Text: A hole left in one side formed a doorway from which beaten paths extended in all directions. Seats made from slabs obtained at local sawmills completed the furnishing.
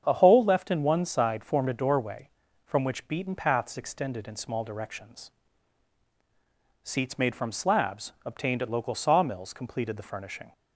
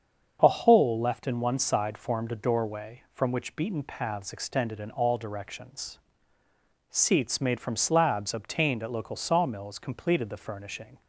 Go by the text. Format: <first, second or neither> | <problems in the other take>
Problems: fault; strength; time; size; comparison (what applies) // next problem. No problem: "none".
second | starts louder than the rest; strong; until 1.0 s; 7.5 dB; also in the second // says "small" for "all"; at 4.3 s